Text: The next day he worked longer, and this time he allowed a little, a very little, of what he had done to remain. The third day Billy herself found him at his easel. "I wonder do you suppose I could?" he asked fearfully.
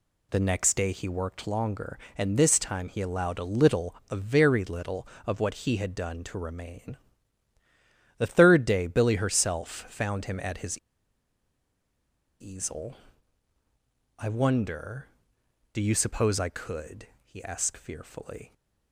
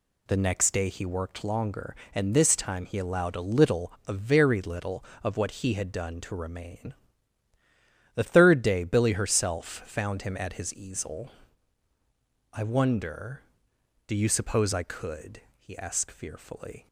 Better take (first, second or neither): second